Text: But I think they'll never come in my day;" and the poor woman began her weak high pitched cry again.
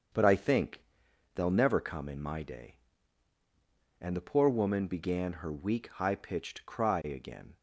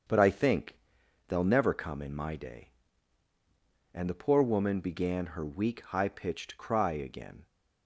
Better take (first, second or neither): neither